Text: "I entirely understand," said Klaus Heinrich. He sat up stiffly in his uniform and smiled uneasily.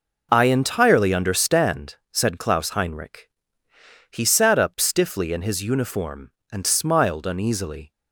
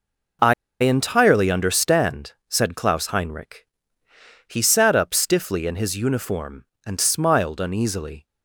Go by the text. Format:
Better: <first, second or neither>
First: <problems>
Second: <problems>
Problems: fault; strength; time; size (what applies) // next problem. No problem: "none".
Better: first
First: none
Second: pauses between "I" and "entirely"; slight; at 0.5 s; 0.28 s long